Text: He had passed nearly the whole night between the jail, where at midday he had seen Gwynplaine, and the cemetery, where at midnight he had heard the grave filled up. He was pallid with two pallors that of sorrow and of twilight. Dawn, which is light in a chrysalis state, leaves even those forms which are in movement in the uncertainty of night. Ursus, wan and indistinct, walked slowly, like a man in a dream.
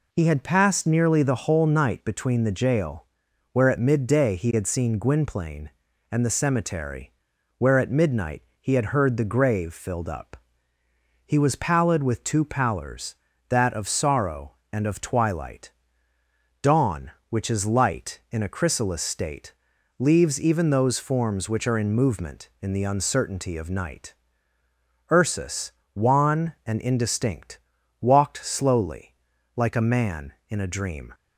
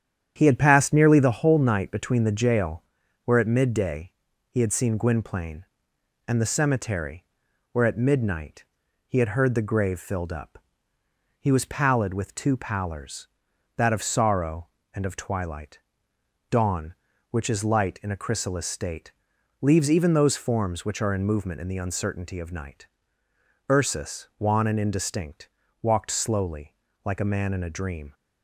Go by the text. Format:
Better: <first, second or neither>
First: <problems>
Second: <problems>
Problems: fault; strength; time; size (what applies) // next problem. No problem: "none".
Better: first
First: pauses between "midnight" and "he"; slight; at 8.4 s; 0.16 s long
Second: starts louder than the rest; strong; until 1.3 s; 9 dB // pauses between "midday" and "he"; at 4.1 s; 0.40 s long // pauses between "midnight" and "he"; at 8.6 s; 0.44 s long